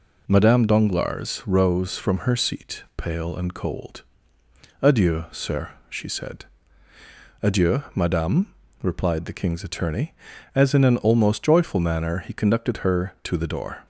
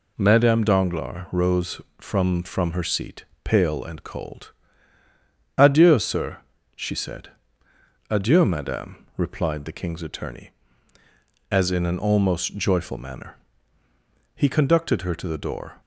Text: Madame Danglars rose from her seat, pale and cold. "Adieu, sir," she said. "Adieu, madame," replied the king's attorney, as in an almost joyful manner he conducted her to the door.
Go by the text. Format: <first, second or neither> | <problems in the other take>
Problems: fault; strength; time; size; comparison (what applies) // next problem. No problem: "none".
first | says "from" twice; at 2.4 s // pauses between "manner" and "he"; at 13.3 s; 1.0 s long